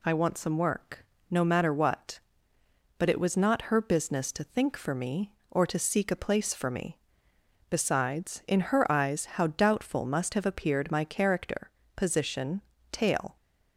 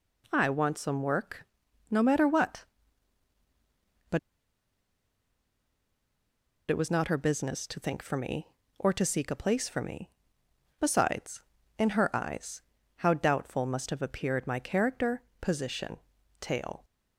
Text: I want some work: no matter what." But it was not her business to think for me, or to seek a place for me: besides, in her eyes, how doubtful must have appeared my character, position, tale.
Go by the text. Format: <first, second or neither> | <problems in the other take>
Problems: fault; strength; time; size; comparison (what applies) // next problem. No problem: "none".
first | pauses between "But" and "it"; strong; at 4.1 s; 2.5 s long